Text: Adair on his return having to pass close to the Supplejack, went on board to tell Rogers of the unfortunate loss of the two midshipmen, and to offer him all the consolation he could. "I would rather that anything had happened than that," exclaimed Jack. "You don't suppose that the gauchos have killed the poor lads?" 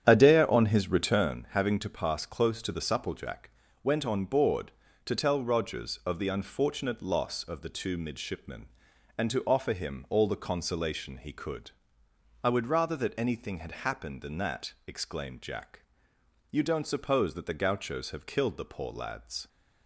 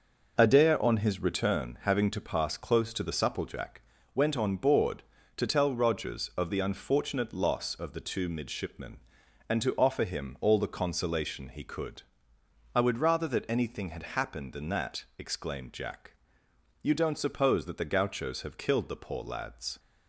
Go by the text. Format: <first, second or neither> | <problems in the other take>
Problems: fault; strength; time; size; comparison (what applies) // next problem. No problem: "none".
second | starts louder than the rest; strong; until 1.5 s; 9.5 dB